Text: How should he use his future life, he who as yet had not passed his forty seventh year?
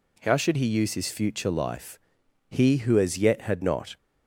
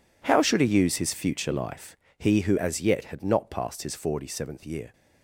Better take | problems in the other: second | stops before "passed his forty seventh year"; at 3.9 s

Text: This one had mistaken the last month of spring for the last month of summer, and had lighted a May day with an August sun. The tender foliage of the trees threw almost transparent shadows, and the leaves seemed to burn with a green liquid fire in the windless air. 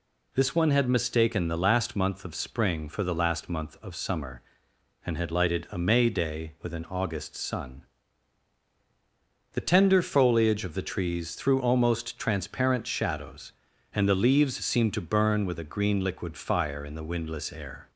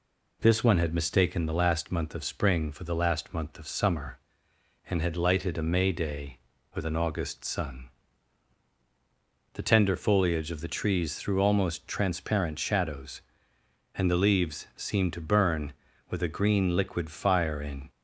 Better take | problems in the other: first | stops before "the windless air"; at 17.8 s

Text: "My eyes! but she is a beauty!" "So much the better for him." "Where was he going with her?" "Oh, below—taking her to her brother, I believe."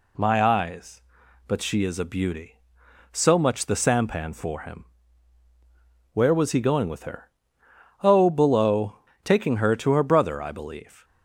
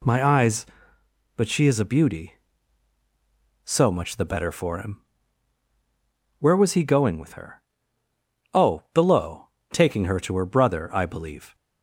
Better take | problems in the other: second | says "sampan" for "better"; at 3.7 s

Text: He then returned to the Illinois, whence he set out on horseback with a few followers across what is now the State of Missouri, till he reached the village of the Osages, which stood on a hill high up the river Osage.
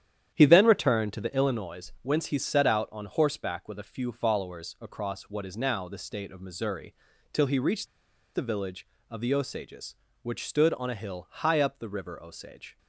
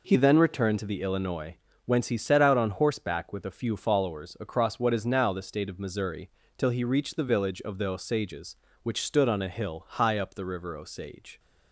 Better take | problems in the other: second | starts louder than the rest; strong; until 1.3 s; 10 dB // pauses between "reached" and "the"; noticeable; at 7.8 s; 0.47 s long

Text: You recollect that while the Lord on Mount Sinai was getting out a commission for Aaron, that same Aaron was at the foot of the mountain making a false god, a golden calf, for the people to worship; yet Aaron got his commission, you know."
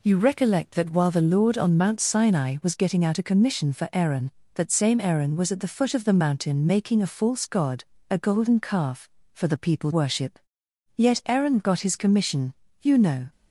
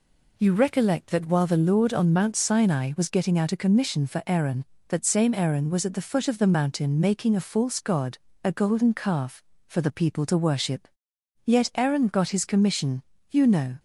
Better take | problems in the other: second | skips "to"; at 9.9 s

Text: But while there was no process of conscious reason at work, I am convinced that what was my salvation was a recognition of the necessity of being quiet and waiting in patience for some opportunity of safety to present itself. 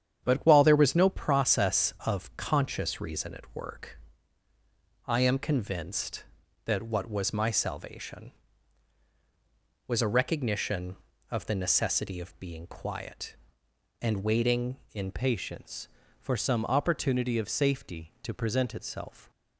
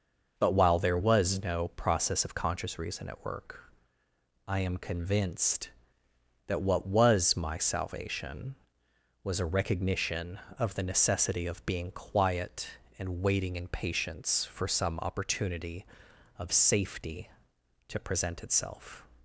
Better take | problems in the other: second | starts louder than the rest; strong; until 1.3 s; 9 dB // changes voice at "patience"; from 15.1 s on; 4.2 s long

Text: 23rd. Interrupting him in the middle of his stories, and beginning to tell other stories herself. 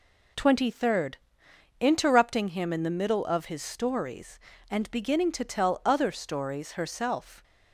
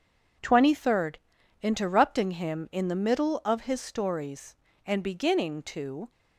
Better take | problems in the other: first | stops before "tell other stories herself"; at 6.1 s

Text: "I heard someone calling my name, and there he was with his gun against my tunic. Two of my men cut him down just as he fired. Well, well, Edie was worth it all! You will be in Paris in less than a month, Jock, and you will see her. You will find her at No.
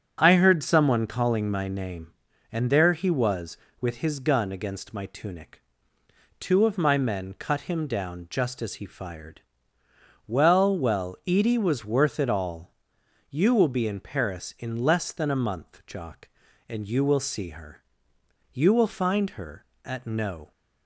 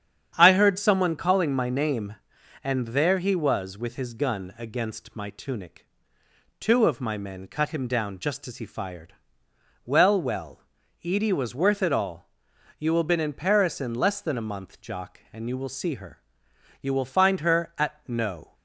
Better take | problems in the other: first | starts louder than the rest; strong; until 1.3 s; 8.5 dB; strong in the first // says "been" for "be"; at 13.0 s

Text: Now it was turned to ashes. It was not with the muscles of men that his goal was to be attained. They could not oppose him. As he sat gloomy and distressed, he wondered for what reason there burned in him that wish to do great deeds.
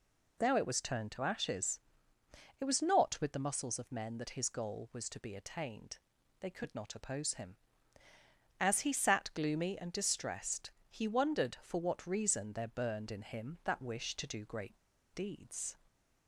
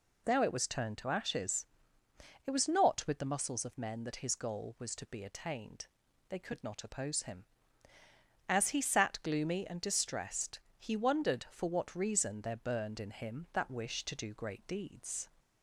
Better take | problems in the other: second | pauses between "great" and "deeds"; at 14.7 s; 0.37 s long

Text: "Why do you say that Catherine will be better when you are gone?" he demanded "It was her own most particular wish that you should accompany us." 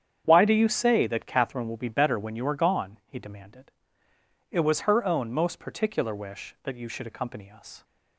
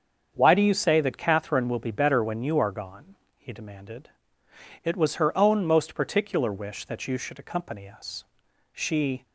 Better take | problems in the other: first | starts louder than the rest; until 1.3 s; 7 dB; strong in the first // pauses between "demanded" and "It"; noticeable; at 4.1 s; 0.70 s long; noticeable in the first // goes on to say "She"; from 8.7 s on; 0.54 s long

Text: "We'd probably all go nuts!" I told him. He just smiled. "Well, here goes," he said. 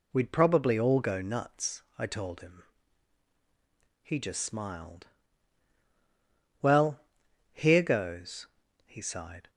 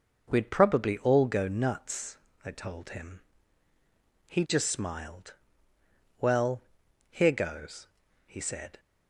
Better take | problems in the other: second | says "sighed" for "said"; at 9.0 s

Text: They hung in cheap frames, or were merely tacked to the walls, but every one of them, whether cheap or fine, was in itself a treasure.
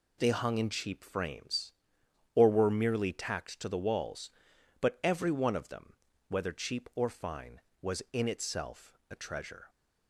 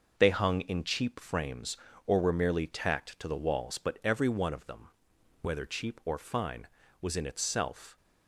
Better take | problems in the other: first | stops before "a treasure"; at 7.9 s

